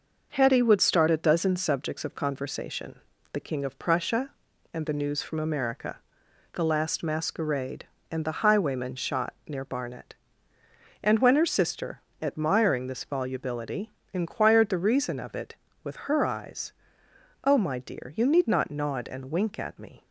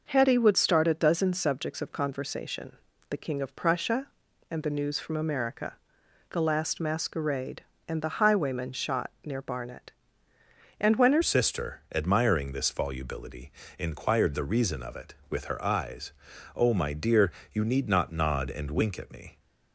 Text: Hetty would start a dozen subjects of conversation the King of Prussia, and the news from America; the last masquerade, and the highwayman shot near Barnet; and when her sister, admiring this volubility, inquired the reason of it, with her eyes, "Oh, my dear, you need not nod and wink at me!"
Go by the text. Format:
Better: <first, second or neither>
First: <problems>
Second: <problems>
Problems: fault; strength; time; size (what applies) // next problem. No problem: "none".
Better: first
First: pauses between "conversation" and "the"; slight; at 2.9 s; 0.32 s long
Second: pauses between "conversation" and "the"; slight; at 2.7 s; 0.32 s long // changes voice at "sister"; from 11.2 s on; 8.1 s long